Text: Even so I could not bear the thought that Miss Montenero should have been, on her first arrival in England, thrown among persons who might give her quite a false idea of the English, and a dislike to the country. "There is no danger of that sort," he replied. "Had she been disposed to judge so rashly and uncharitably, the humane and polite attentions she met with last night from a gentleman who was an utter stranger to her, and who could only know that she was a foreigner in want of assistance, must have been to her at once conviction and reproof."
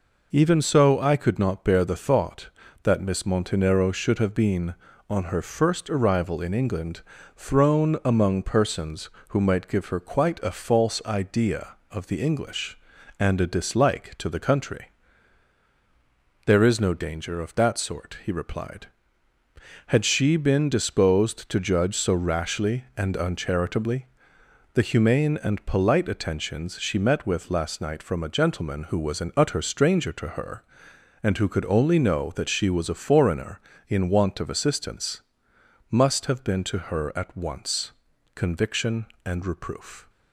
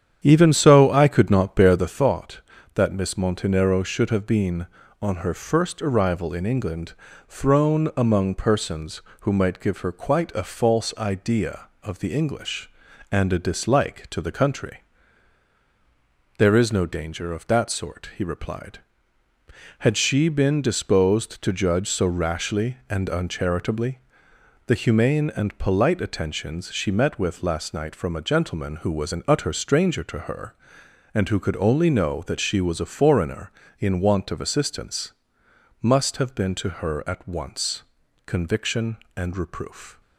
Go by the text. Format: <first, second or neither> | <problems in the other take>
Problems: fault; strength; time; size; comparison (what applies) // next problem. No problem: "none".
first | starts louder than the rest; strong; until 1.9 s; 9 dB // pauses between "once" and "conviction"; at 37.8 s; 0.44 s long; also in the first